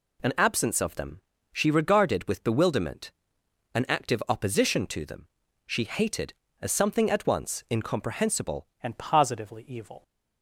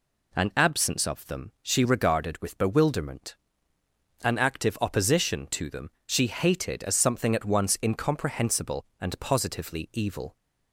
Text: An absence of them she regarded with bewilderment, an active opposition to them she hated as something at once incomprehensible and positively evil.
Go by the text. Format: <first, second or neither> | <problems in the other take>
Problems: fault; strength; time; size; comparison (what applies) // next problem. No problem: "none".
second | pauses between "them" and "she"; slight; at 1.2 s; 0.32 s long // pauses between "them" and "she"; at 5.2 s; 0.38 s long; slight in the second // changes voice at "and"; from 8.8 s on; 1.2 s long